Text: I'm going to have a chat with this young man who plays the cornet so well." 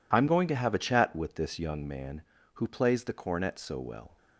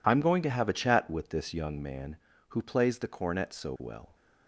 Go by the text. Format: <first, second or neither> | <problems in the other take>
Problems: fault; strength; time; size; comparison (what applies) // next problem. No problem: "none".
neither | none